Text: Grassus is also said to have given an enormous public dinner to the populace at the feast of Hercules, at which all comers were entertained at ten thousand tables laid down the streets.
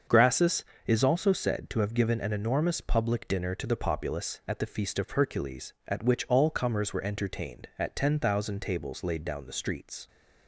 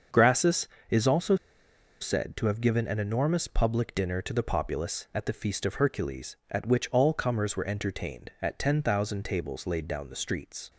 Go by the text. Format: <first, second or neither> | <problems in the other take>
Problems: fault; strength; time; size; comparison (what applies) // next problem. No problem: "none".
first | starts louder than the rest; until 1.3 s; 6.5 dB; also in the first // pauses between "also" and "said"; noticeable; at 1.3 s; 0.66 s long